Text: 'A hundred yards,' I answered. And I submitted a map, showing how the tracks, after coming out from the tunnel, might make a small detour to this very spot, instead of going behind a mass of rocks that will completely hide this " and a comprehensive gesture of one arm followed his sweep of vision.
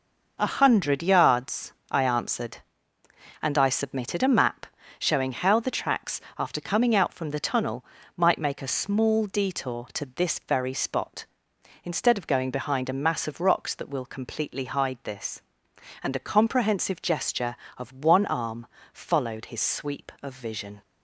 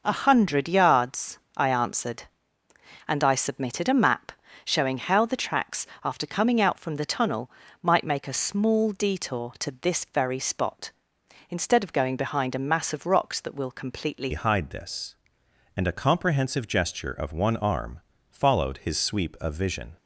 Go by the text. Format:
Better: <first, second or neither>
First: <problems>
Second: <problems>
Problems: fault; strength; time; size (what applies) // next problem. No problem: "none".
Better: first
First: pauses between "arm" and "followed"; slight; at 18.6 s; 0.28 s long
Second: changes voice at "hide"; from 14.3 s on; 5.6 s long // pauses between "arm" and "followed"; slight; at 18.0 s; 0.30 s long